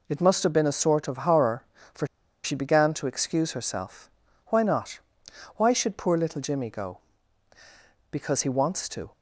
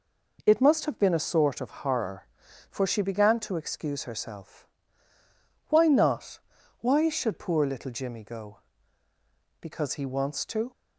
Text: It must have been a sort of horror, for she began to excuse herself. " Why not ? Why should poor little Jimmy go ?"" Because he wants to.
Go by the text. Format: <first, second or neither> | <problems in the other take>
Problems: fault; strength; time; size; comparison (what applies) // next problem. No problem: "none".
second | pauses between "for" and "she"; at 2.0 s; 0.38 s long